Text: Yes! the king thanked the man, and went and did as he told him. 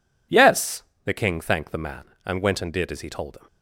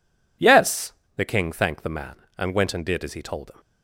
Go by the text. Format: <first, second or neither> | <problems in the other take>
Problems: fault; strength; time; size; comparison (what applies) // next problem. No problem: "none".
neither | none